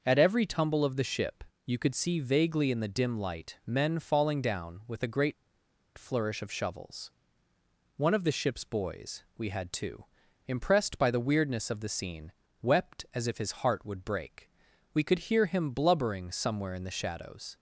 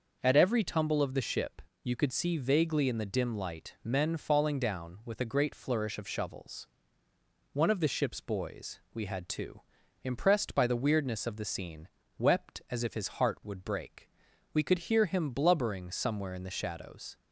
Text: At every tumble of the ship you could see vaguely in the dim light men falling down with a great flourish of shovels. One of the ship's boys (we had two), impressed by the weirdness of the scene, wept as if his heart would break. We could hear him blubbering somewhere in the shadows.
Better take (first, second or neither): second